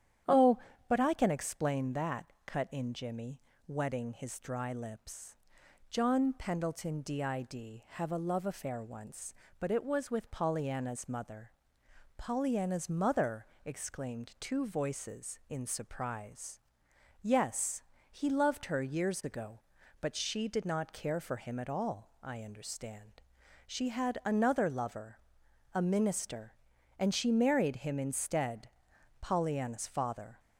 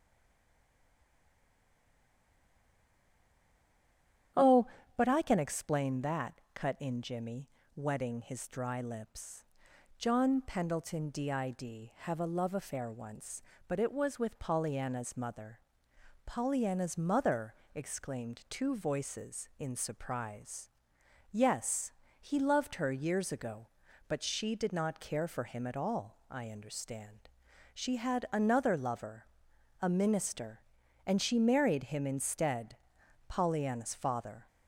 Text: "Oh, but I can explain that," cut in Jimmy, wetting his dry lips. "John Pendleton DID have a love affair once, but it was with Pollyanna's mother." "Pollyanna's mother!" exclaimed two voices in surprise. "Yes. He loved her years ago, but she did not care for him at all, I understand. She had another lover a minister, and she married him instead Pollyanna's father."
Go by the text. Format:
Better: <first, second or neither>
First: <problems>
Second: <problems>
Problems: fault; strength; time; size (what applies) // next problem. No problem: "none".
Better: first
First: starts louder than the rest; strong; until 1.5 s; 10 dB // pauses between "lover" and "a"; noticeable; at 25.1 s; 0.54 s long // pauses between "instead" and "Pollyanna's"; noticeable; at 28.6 s; 0.50 s long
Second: stays silent before the first word; strong; until 4.3 s; 4.3 s long // starts louder than the rest; strong; until 5.6 s; 10 dB // pauses between "lover" and "a"; noticeable; at 29.2 s; 0.54 s long // pauses between "instead" and "Pollyanna's"; noticeable; at 32.7 s; 0.50 s long